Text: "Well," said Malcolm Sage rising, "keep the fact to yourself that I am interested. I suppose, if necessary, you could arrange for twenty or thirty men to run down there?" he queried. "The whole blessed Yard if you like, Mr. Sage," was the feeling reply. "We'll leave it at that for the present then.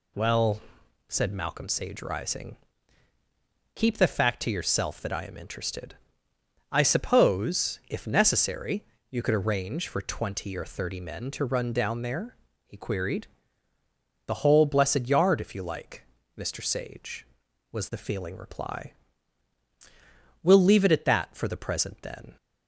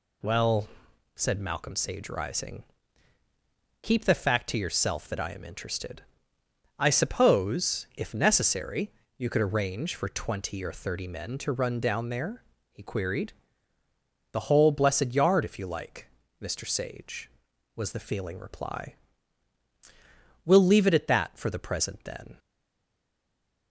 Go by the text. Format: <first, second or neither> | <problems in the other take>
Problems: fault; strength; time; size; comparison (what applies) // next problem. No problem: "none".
first | stays silent after the last word; noticeable; from 22.3 s on; 1.3 s long